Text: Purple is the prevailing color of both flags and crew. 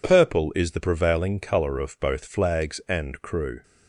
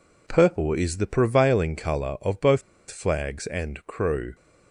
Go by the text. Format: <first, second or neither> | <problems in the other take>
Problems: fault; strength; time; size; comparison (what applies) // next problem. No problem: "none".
first | pauses between "both" and "flags"; slight; at 2.6 s; 0.29 s long